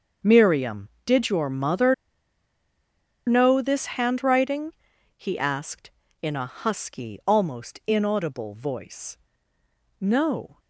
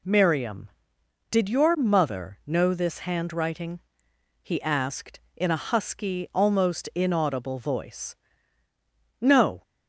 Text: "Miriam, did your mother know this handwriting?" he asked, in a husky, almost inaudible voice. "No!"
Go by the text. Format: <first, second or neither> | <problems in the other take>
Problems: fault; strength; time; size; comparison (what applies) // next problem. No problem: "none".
second | starts louder than the rest; until 1.3 s; 6.5 dB // pauses between "mother" and "know"; strong; at 1.9 s; 1.3 s long